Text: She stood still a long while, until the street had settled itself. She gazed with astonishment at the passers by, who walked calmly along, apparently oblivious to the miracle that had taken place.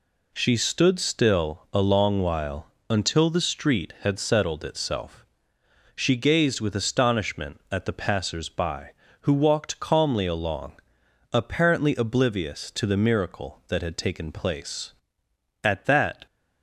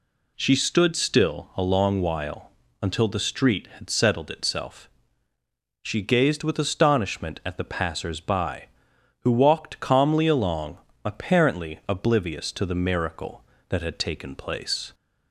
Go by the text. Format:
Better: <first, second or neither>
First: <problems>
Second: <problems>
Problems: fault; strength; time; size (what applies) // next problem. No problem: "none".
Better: second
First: goes on to say "At that"; noticeable; from 15.6 s on; 0.64 s long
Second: none